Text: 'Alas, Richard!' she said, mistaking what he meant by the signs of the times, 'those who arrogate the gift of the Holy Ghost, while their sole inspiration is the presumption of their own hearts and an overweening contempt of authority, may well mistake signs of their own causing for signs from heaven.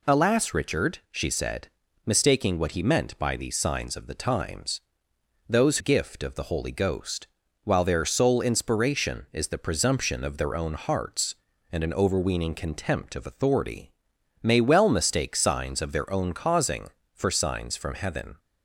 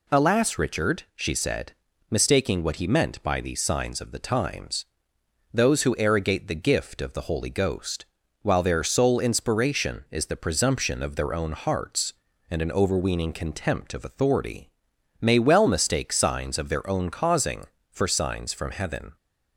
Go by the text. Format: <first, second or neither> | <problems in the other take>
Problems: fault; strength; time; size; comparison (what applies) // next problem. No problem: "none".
second | skips "who arrogate the"; at 5.7 s